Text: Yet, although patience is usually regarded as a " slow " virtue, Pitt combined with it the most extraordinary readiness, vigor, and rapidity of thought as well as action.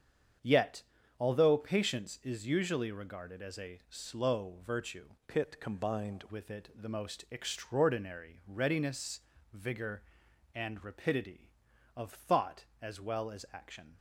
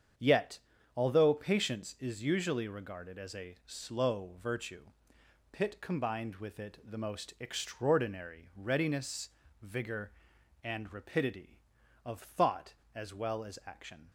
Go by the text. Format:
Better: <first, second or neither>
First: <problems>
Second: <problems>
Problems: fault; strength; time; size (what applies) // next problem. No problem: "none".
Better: second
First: starts louder than the rest; strong; until 1.7 s; 8 dB // changes voice from "Pitt" to "combined"; from 5.2 to 6.2 s; 1.0 s long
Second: starts louder than the rest; strong; until 1.5 s; 7.5 dB